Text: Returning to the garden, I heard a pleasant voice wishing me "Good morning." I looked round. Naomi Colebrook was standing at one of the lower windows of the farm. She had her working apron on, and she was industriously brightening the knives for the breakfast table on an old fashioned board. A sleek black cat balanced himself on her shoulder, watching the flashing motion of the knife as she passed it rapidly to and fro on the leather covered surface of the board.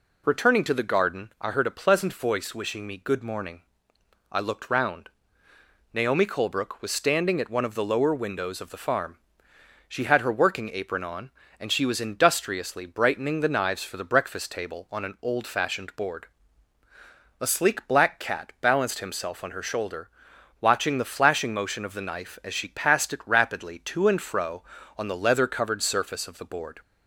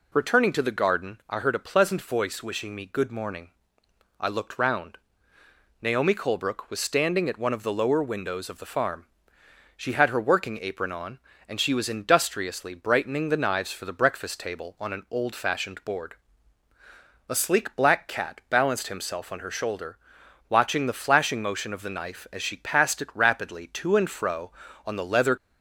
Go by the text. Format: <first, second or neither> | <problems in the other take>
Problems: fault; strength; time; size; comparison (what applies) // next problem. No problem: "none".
first | stops before "covered surface of the board"; at 25.3 s